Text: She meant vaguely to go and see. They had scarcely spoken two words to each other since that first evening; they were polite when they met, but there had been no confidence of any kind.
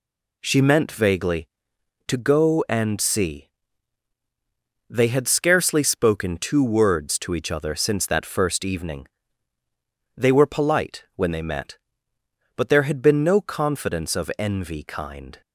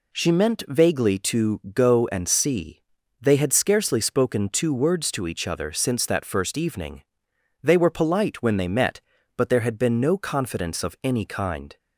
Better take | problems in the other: second | says "envy" for "any"; at 14.3 s

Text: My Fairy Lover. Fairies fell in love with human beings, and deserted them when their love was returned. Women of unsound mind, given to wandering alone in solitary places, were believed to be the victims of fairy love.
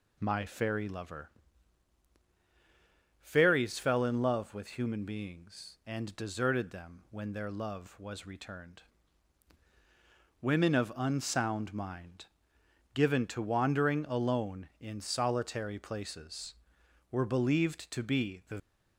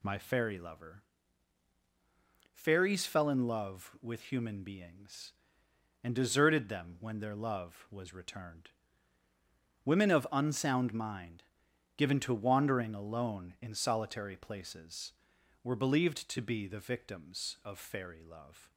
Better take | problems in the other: second | stops before "victims of fairy love"; at 18.5 s

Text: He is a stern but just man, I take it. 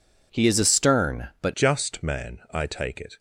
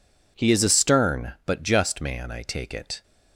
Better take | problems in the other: second | changes voice at "just"; from 1.5 s on; 1.6 s long

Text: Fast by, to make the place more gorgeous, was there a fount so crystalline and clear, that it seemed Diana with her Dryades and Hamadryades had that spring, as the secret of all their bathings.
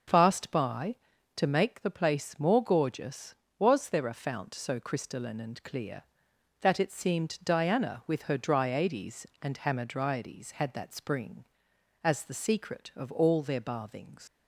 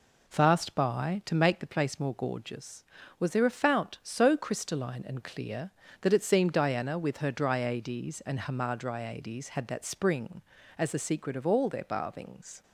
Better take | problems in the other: second | starts louder than the rest; until 1.5 s; 6.5 dB // leaves "bathings" unfinished; at 14.2 s; 70 ms

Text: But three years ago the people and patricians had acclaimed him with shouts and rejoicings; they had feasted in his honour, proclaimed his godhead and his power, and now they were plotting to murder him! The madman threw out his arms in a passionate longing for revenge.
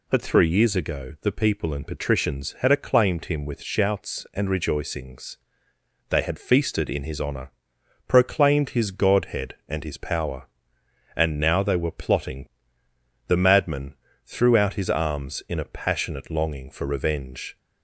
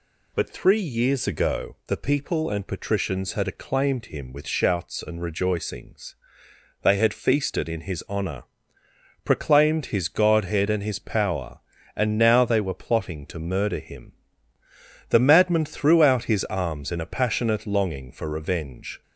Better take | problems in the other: second | skips "to murder him"; at 12.8 s // pauses between "madman" and "threw"; slight; at 13.9 s; 0.32 s long

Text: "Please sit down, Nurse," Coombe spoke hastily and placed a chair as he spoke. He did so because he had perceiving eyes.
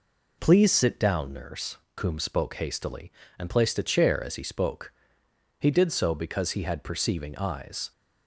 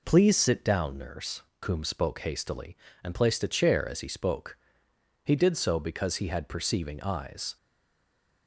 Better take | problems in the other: first | stays silent after the last word; slight; from 7.5 s on; 0.9 s long

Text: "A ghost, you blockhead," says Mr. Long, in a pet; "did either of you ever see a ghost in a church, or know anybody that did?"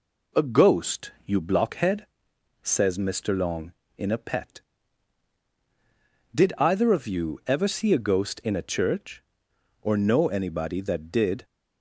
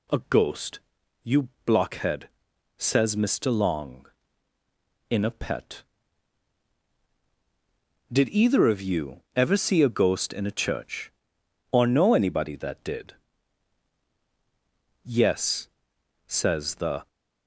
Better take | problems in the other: first | pauses between "you" and "blockhead"; slight; at 1.4 s; 0.16 s long // goes on to say "Yes says the"; strong; from 15.0 s on; 2.0 s long

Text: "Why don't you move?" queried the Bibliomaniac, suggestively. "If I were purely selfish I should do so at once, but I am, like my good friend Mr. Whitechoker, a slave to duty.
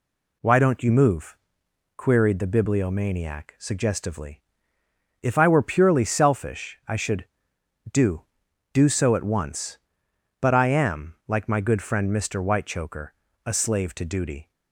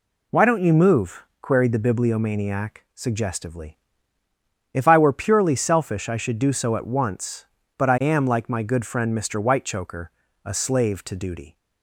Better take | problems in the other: second | says "do" twice; at 8.7 s

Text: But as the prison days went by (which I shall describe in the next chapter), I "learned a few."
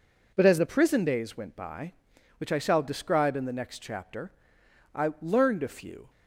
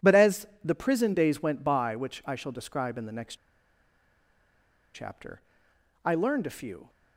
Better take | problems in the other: first | pauses between "as" and "the"; slight; at 0.4 s; 0.16 s long // pauses between "next" and "chapter"; strong; at 3.3 s; 1.5 s long

